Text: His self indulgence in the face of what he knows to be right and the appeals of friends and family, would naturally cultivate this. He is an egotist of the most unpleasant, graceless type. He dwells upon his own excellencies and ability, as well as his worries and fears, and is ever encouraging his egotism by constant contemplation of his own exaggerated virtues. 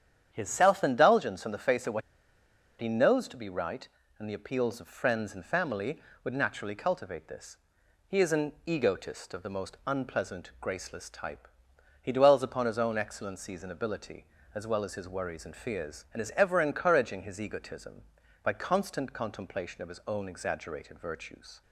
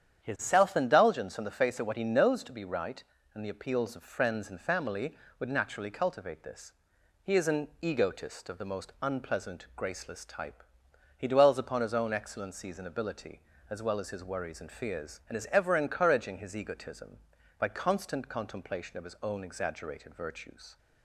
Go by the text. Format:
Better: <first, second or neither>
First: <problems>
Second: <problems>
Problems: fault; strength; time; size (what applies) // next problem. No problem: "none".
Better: second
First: starts louder than the rest; strong; until 1.3 s; 9 dB // pauses between "what" and "he"; noticeable; at 2.0 s; 0.80 s long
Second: starts louder than the rest; strong; until 1.2 s; 9 dB